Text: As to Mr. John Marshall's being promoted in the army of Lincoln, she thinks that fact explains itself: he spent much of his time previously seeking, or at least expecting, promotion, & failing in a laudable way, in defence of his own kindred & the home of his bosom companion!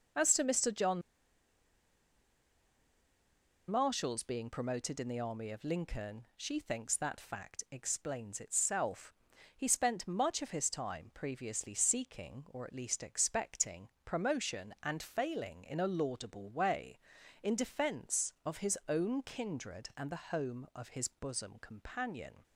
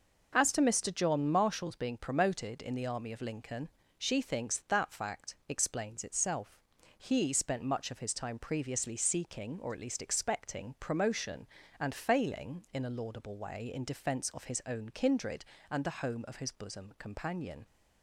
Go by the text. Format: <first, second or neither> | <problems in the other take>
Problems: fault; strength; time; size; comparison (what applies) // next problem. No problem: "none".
second | starts louder than the rest; noticeable; until 3.8 s; 6 dB // pauses between "John" and "Marshall's"; strong; at 1.0 s; 2.6 s long